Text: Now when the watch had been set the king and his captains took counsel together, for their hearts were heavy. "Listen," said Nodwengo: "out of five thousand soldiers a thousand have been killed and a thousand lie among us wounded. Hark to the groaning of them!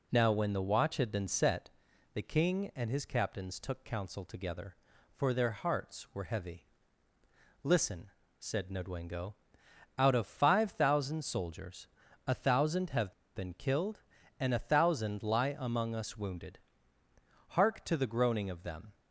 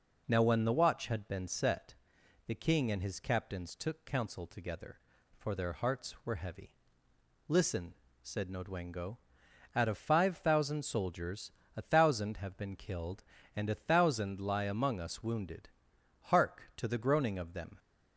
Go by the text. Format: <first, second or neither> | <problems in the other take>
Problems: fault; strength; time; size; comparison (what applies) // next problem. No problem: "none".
second | pauses between "set" and "the"; at 1.7 s; 0.44 s long; noticeable in the second // pauses between "soldiers" and "a"; at 11.8 s; 0.40 s long; slight in the second // pauses between "have" and "been"; slight; at 13.1 s; 0.23 s long